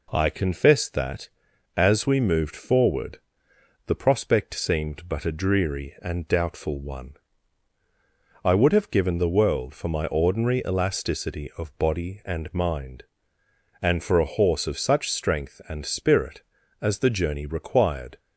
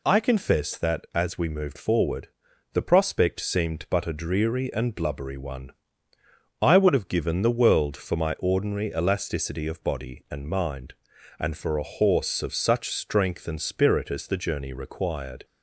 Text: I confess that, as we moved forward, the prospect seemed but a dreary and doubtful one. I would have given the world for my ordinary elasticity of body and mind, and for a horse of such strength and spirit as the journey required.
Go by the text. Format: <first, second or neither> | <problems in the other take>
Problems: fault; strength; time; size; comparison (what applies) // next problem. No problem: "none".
first | says "blubbery" for "doubtful"; at 4.9 s